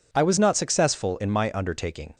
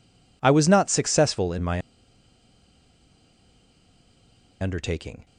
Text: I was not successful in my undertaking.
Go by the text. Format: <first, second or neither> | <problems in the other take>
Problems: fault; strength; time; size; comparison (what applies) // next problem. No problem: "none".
first | pauses between "my" and "undertaking"; strong; at 1.8 s; 2.8 s long